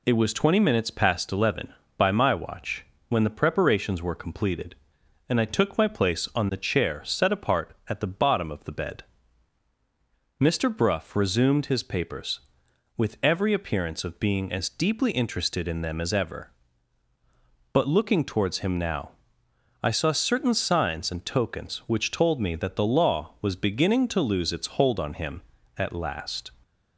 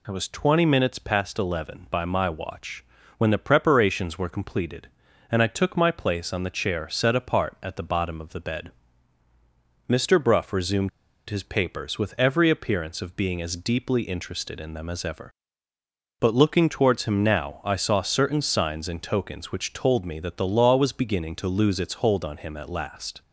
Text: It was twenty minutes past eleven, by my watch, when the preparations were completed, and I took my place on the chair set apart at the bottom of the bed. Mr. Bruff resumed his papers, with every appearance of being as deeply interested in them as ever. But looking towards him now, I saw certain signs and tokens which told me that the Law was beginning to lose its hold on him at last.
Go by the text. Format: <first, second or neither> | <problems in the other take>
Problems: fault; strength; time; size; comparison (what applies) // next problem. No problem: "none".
first | pauses between "resumed" and "his"; at 10.8 s; 0.39 s long